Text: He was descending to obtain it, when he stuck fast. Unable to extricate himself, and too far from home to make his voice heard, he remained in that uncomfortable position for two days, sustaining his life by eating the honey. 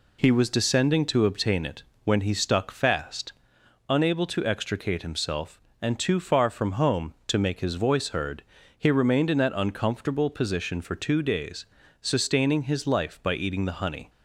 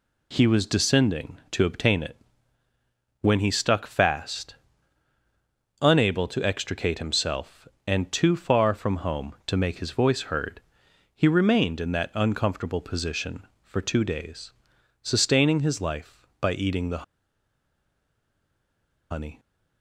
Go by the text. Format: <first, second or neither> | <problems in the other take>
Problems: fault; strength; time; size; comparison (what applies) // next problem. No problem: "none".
first | pauses between "the" and "honey"; strong; at 17.0 s; 2.0 s long